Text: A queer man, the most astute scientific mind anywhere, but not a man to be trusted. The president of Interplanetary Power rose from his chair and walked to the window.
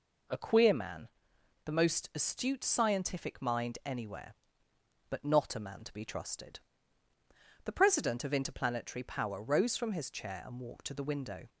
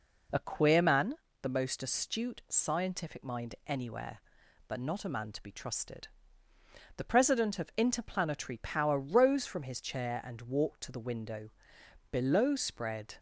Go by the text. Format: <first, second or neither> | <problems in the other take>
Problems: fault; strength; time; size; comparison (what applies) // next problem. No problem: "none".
first | goes on to say "Below spread"; noticeable; from 12.1 s on; 1.0 s long